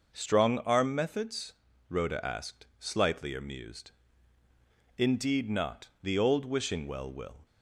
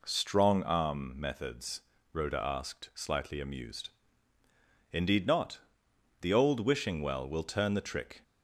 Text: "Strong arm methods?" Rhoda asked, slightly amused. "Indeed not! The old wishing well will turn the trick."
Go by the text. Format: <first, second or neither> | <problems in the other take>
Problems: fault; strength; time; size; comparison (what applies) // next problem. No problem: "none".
second | stops before "turn the trick"; at 7.4 s